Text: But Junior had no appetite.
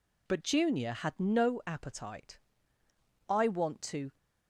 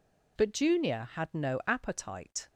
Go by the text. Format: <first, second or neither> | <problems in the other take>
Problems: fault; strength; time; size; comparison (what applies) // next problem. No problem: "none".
second | goes on to say "I want to"; noticeable; from 3.2 s on; 0.86 s long